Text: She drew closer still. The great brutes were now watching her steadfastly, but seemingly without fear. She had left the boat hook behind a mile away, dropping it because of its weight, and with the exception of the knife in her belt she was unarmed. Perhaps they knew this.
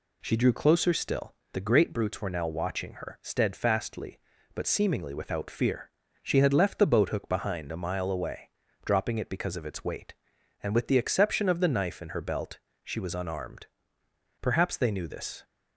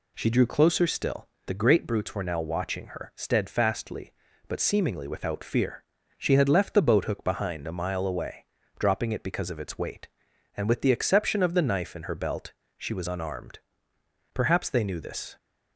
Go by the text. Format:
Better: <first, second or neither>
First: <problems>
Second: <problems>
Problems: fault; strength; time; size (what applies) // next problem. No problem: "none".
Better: neither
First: pauses between "belt" and "she"; slight; at 12.5 s; 0.24 s long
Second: pauses between "belt" and "she"; slight; at 12.5 s; 0.24 s long